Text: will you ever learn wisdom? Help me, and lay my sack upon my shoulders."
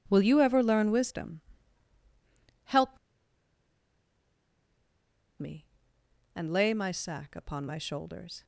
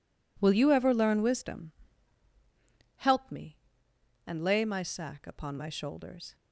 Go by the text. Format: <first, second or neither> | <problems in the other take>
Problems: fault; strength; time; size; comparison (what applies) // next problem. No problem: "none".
second | pauses between "Help" and "me"; strong; at 2.9 s; 2.4 s long